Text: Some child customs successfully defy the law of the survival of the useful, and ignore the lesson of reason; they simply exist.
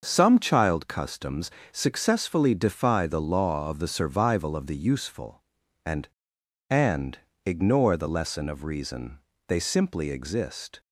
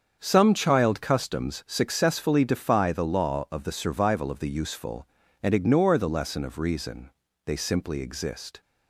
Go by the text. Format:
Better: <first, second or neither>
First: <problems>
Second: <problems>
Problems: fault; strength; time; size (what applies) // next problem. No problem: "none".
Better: second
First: starts louder than the rest; noticeable; until 1.0 s; 6 dB // pauses between "customs" and "successfully"; slight; at 1.4 s; 0.22 s long // says "and" twice; at 6.6 s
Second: starts louder than the rest; strong; until 1.2 s; 7 dB